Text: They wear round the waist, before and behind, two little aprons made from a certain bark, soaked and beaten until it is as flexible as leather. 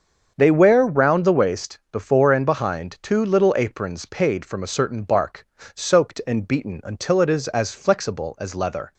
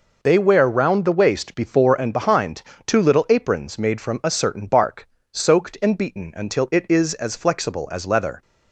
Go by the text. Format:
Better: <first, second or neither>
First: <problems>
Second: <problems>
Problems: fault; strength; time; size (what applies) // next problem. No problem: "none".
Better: second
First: starts louder than the rest; until 1.3 s; 7 dB // says "paid" for "made"; at 4.0 s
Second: none